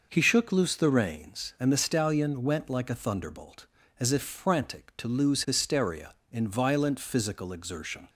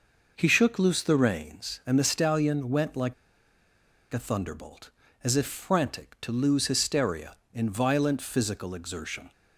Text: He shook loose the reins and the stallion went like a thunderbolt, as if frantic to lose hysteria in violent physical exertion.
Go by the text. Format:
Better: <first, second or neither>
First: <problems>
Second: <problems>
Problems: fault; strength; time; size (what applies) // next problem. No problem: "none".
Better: first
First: none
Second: pauses between "like" and "a"; at 3.1 s; 0.98 s long